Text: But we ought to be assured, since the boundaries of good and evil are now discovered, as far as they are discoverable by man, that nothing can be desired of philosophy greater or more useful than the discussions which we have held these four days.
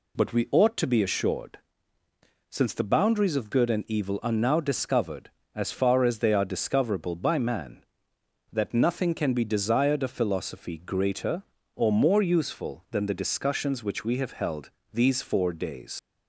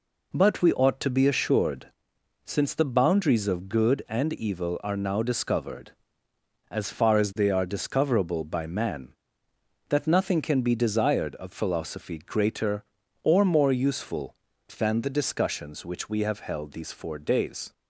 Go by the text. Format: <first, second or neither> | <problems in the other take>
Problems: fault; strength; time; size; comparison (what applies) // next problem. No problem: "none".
second | pauses between "held" and "these"; slight; at 14.7 s; 0.22 s long // leaves "days" unfinished; at 15.9 s; 75 ms